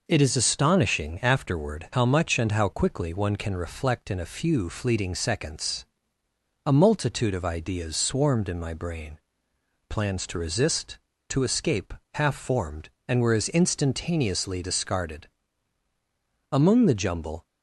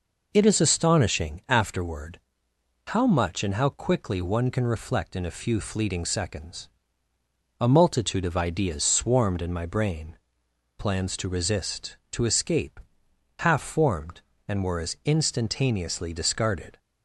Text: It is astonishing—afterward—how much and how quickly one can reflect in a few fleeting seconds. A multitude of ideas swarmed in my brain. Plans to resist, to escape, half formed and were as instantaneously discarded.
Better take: second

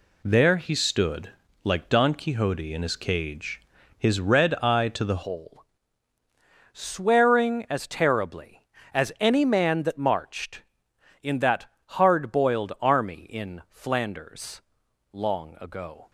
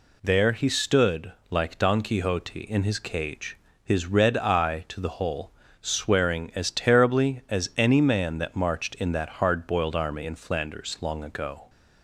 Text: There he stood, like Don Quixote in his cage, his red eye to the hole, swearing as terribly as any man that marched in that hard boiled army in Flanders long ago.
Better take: second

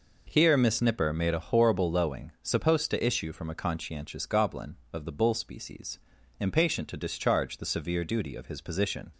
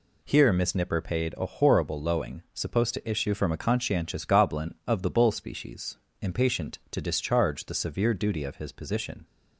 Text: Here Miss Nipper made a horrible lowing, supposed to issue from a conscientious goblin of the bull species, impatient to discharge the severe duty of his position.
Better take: first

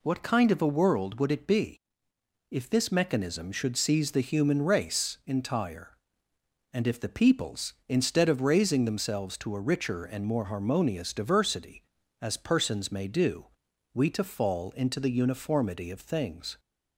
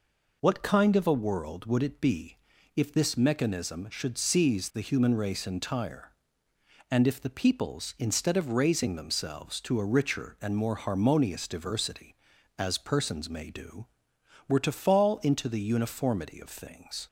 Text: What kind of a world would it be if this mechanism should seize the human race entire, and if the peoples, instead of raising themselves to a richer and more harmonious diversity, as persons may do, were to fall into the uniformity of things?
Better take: second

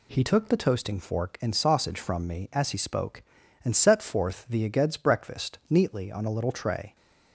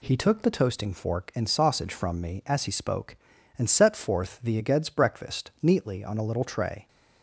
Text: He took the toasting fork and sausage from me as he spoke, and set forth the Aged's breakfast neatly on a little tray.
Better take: neither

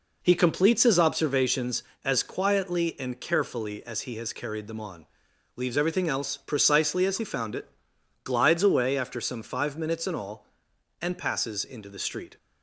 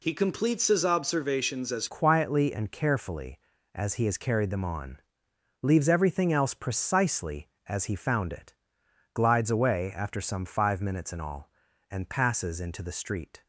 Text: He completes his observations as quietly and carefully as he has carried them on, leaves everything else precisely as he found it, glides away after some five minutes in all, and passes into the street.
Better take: first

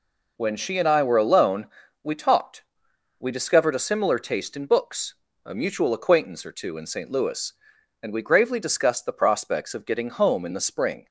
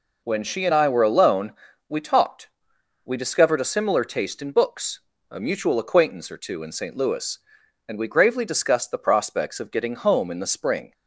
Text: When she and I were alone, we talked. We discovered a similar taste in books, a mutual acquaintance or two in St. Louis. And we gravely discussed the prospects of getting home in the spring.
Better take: neither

